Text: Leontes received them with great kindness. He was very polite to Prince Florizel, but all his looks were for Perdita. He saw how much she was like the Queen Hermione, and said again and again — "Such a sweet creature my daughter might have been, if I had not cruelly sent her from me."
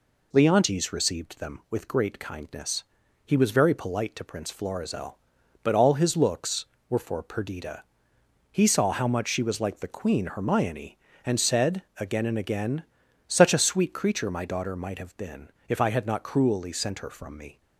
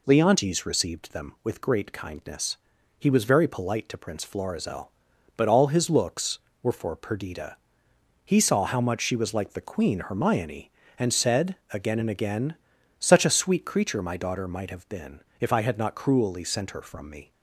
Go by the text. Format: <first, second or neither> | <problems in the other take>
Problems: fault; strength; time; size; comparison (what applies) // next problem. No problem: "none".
neither | pauses between "said" and "again"; slight; the same in both